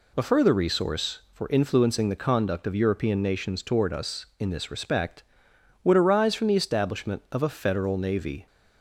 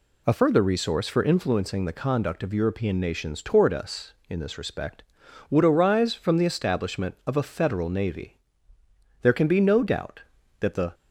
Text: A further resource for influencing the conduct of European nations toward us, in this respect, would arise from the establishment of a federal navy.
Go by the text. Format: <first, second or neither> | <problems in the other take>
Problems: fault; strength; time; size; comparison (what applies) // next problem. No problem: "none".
first | goes on to say "There can be no doubt that the"; strong; from 9.2 s on; 1.7 s long